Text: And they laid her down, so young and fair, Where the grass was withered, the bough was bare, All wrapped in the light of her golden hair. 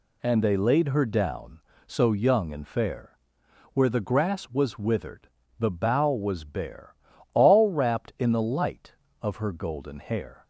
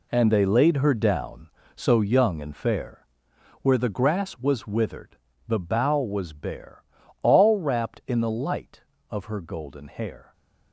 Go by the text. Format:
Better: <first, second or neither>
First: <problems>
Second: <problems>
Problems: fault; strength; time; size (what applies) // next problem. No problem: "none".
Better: first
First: none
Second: gets quieter; strong; throughout; 10 dB